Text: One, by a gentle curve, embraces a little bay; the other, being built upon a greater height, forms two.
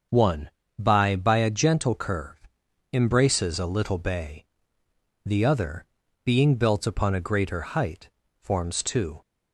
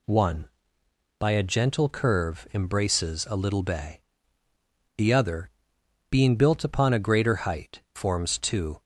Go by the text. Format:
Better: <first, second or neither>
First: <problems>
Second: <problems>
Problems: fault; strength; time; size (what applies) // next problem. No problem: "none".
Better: second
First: starts louder than the rest; until 1.3 s; 6.5 dB // says "by" twice; at 1.1 s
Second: none